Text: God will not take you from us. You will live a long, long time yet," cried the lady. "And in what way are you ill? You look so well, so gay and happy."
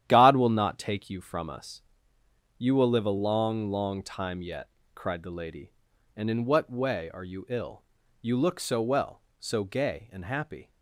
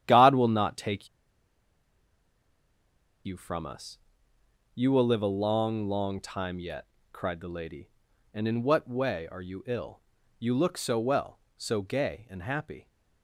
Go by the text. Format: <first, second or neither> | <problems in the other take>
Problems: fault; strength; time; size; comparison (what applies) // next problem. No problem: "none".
first | starts louder than the rest; strong; until 1.0 s; 10.5 dB; strong in the first // pauses between "take" and "you"; strong; at 1.0 s; 2.1 s long